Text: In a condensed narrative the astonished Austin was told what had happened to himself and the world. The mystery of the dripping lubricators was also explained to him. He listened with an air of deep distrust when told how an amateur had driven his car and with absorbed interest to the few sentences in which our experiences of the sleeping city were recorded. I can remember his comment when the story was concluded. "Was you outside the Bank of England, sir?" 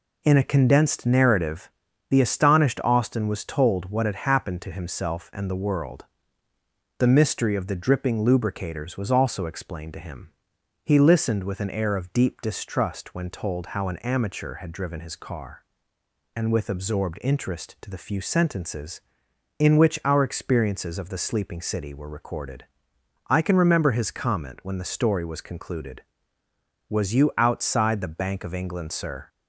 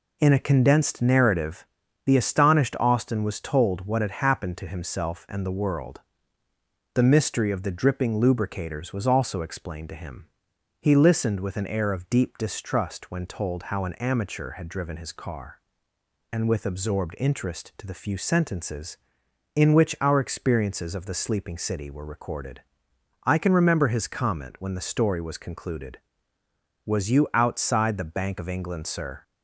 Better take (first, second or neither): neither